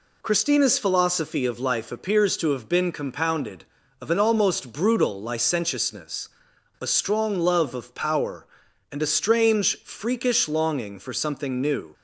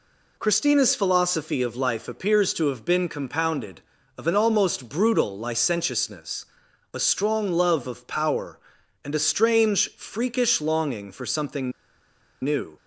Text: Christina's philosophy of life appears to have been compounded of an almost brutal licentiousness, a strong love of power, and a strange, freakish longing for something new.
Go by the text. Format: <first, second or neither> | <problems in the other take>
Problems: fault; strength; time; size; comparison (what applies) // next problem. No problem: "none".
first | pauses between "something" and "new"; noticeable; at 11.7 s; 0.72 s long